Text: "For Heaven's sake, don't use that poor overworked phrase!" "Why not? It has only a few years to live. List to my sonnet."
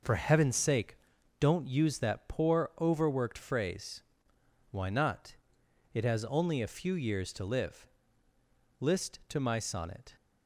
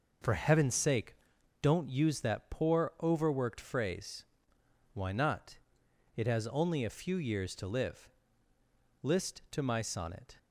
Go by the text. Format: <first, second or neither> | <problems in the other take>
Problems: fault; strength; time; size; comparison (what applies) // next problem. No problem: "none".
neither | none